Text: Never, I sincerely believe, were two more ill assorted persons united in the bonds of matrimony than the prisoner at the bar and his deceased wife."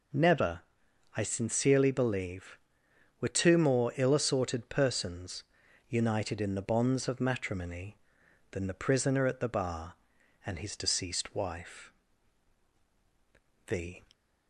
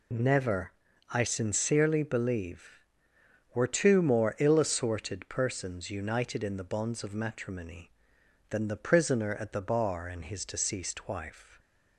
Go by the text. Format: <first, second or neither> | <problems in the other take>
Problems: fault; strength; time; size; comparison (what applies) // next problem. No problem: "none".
second | pauses between "persons" and "united"; at 5.4 s; 0.44 s long // goes on to say "The"; slight; from 13.6 s on; 0.38 s long